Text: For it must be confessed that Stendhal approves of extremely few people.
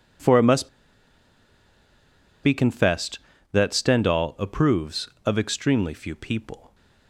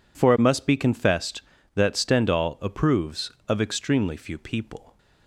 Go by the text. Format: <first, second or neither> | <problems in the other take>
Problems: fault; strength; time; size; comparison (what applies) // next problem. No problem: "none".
second | pauses between "must" and "be"; strong; at 0.6 s; 1.7 s long